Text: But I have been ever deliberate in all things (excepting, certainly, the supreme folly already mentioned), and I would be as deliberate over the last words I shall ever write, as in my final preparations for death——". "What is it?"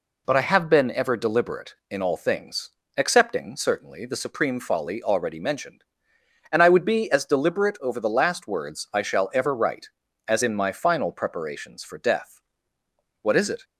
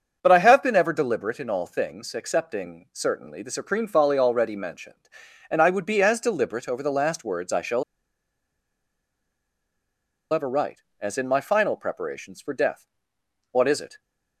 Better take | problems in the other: first | starts louder than the rest; until 1.2 s; 7 dB // pauses between "shall" and "ever"; strong; at 7.8 s; 2.5 s long

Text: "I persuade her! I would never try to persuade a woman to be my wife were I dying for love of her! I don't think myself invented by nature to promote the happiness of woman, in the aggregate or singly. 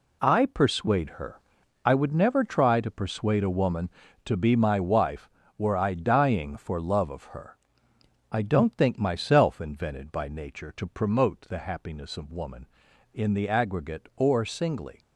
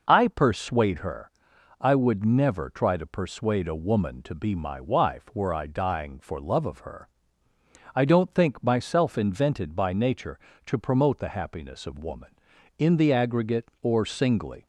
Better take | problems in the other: neither | none

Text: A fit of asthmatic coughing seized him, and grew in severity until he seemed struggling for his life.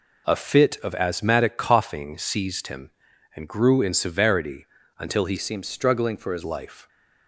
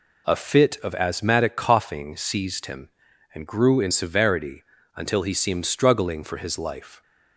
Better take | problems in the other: second | pauses between "severity" and "until"; slight; at 4.6 s; 0.34 s long; slight in the second // changes voice from "seemed" to "his"; from 5.3 to 6.4 s; 1.1 s long

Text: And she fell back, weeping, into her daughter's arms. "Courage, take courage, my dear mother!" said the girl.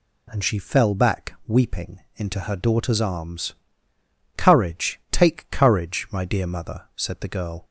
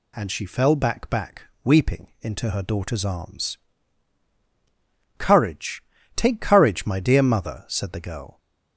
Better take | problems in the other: first | says "back" twice; at 1.1 s

